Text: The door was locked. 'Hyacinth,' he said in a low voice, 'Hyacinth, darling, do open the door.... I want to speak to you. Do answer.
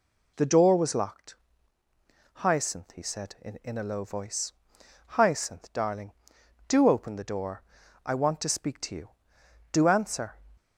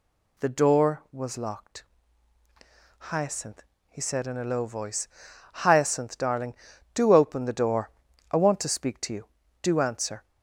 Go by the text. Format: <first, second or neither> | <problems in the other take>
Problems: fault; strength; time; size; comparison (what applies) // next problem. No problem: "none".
second | says "in" twice; at 3.6 s